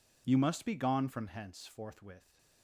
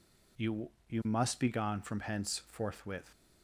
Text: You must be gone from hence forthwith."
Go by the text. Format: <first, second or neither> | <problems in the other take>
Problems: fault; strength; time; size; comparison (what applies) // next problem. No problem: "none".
first | says "You" twice; at 0.9 s